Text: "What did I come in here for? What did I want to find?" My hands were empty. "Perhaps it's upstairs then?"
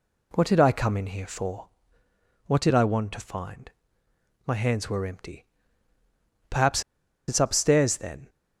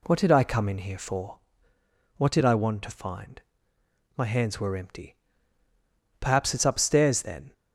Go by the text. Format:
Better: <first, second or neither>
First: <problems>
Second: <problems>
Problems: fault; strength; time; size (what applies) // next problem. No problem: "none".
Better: second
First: pauses between "Perhaps" and "it's"; noticeable; at 6.8 s; 0.46 s long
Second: none